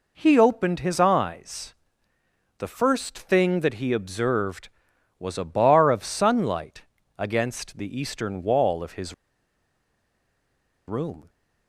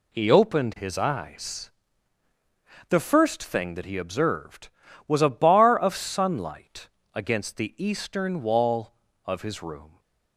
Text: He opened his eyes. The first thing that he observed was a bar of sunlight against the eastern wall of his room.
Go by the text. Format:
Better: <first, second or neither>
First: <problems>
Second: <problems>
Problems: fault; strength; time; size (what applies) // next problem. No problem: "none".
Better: second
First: pauses between "sunlight" and "against"; slight; at 6.8 s; 0.32 s long // pauses between "his" and "room"; strong; at 9.1 s; 1.7 s long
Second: pauses between "sunlight" and "against"; slight; at 6.8 s; 0.26 s long